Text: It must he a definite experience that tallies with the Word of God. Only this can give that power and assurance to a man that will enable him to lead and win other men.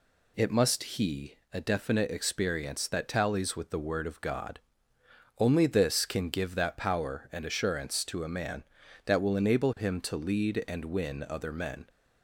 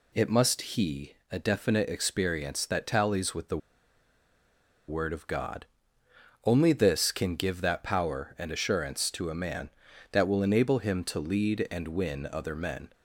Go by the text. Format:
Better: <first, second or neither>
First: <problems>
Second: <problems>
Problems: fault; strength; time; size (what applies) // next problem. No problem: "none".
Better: first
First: pauses between "he" and "a"; slight; at 1.3 s; 0.18 s long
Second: pauses between "he" and "a"; slight; at 1.1 s; 0.18 s long // pauses between "the" and "Word"; strong; at 3.5 s; 1.3 s long